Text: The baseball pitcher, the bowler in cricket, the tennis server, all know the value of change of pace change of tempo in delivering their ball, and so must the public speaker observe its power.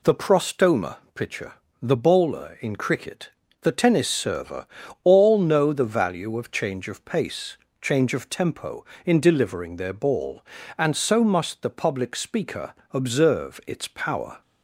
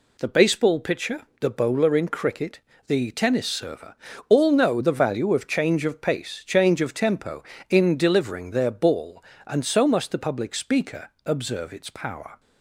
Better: second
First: says "prostoma" for "baseball"; at 0.1 s // pauses between "pace" and "change"; slight; at 7.5 s; 0.26 s long // pauses between "speaker" and "observe"; slight; at 12.7 s; 0.20 s long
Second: pauses between "speaker" and "observe"; slight; at 11.0 s; 0.16 s long

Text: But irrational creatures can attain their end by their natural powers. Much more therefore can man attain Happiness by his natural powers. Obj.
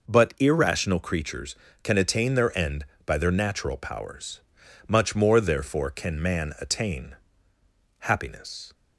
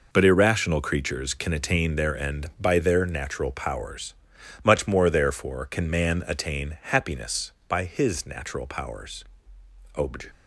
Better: second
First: pauses between "attain" and "Happiness"; noticeable; at 7.1 s; 0.84 s long // stops before "by his natural powers Obj"; at 8.7 s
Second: none

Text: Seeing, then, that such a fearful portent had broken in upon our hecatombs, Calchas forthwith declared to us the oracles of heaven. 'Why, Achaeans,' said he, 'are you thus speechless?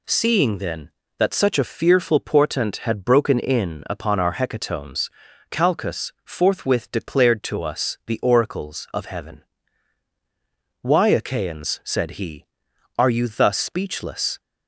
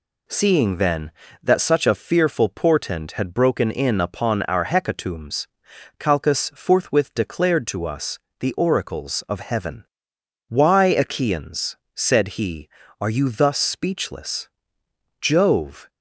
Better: first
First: none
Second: pauses between "us" and "the"; slight; at 8.1 s; 0.22 s long // goes on to say "Jove"; noticeable; from 15.2 s on; 0.68 s long

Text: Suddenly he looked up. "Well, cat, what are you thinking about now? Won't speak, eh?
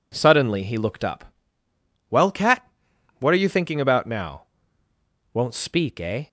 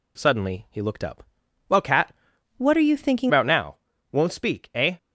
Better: first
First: none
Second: changes voice from "what" to "thinking"; from 2.5 to 3.3 s; 0.8 s long

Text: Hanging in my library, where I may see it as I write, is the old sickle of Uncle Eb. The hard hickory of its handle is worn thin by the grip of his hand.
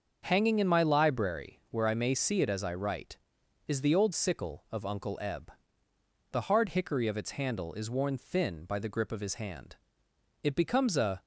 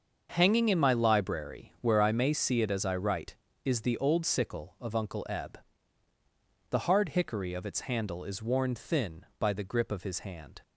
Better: second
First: starts louder than the rest; until 1.2 s; 6.5 dB // goes on to say "It becomes a"; noticeable; from 10.4 s on; 0.78 s long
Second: starts louder than the rest; until 1.3 s; 6.5 dB

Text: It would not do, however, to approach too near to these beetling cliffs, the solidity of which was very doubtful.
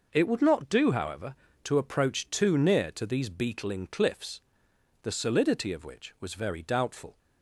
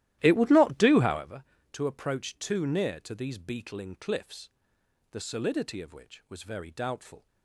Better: first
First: none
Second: starts louder than the rest; strong; until 1.3 s; 14 dB

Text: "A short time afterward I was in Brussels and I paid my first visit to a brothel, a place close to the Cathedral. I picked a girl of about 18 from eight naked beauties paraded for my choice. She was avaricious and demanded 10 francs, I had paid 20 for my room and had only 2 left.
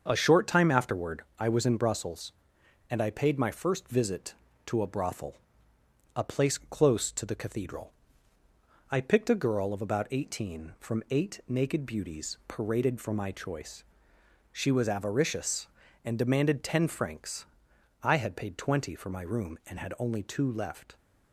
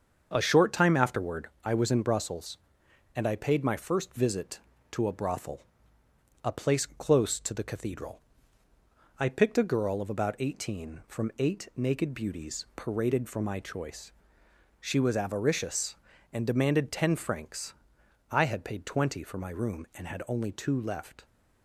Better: neither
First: starts louder than the rest; until 1.0 s; 7 dB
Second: starts louder than the rest; until 1.3 s; 7 dB

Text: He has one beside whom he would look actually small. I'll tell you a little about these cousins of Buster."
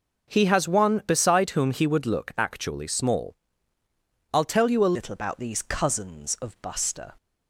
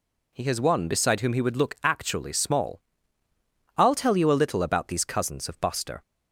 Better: second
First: changes voice at "little"; from 4.9 s on; 2.2 s long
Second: none

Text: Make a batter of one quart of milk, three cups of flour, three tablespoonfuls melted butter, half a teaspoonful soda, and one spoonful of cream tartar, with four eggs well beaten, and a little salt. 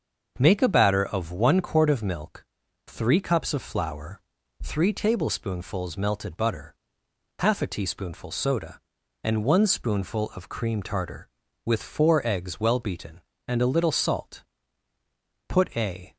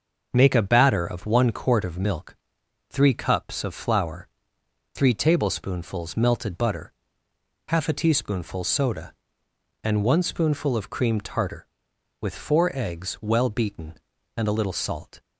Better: second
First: starts louder than the rest; until 1.4 s; 6.5 dB // goes on to say "Put a"; noticeable; from 15.4 s on; 0.68 s long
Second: starts louder than the rest; noticeable; until 1.3 s; 6 dB

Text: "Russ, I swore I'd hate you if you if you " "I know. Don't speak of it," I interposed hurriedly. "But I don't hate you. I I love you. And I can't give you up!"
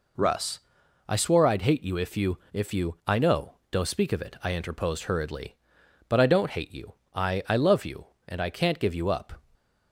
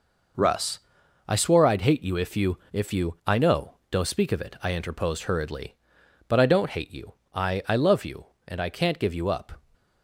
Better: first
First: pauses between "you" and "if"; slight; at 2.3 s; 0.16 s long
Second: gets quieter; strong; throughout; 8 dB // pauses between "you" and "if"; slight; at 2.5 s; 0.16 s long

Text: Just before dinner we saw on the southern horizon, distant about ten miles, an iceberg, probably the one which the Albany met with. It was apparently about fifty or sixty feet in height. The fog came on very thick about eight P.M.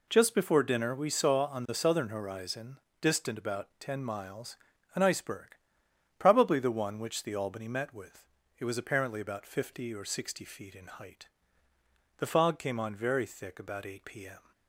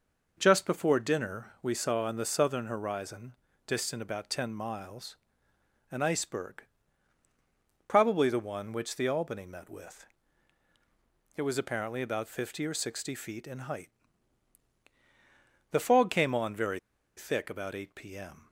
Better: first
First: none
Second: pauses between "very" and "thick"; at 16.7 s; 0.38 s long

